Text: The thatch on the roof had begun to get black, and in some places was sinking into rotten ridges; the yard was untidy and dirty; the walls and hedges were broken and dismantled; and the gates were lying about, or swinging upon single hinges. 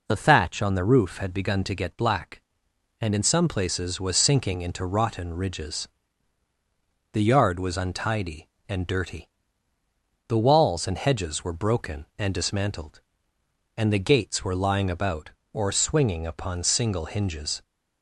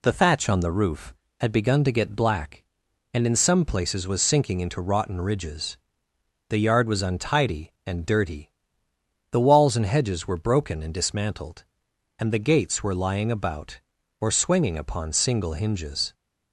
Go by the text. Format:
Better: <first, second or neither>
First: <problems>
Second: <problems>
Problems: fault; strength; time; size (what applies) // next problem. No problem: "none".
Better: neither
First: none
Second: none